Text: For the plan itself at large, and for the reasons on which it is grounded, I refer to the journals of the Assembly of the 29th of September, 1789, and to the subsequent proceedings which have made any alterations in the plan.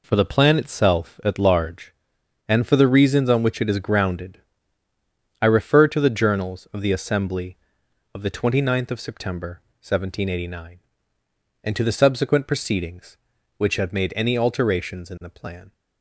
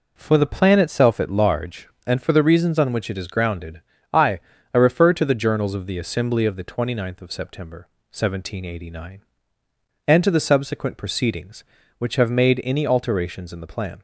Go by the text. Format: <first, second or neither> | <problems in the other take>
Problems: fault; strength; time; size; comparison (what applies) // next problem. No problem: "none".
first | says "I" twice; at 4.7 s